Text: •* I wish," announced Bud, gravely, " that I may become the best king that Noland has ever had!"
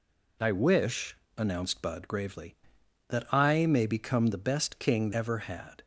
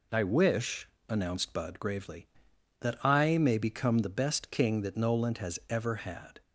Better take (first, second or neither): second